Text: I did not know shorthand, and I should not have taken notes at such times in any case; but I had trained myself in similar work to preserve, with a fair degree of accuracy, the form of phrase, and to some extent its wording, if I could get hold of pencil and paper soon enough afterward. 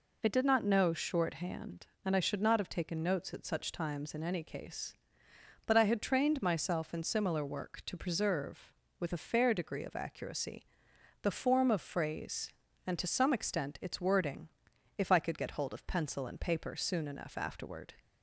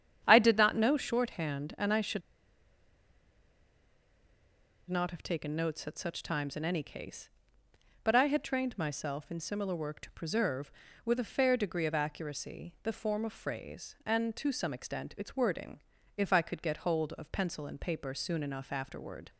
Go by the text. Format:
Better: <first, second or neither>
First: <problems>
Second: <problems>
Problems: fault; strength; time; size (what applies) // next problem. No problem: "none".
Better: first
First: none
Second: starts louder than the rest; strong; until 1.2 s; 8.5 dB // pauses between "should" and "not"; strong; at 2.2 s; 2.6 s long